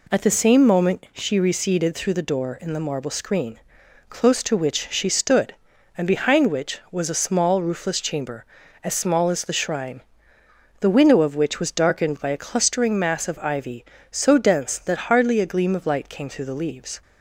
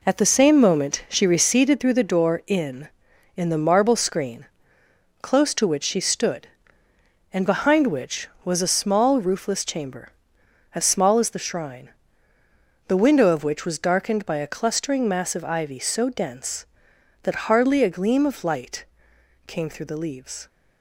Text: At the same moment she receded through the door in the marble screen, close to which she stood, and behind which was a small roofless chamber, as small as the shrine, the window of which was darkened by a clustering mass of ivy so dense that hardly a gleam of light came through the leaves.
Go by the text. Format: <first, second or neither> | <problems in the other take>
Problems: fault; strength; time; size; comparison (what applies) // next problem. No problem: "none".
first | says "in" twice; at 3.3 s // pauses between "light" and "came"; noticeable; at 18.8 s; 0.64 s long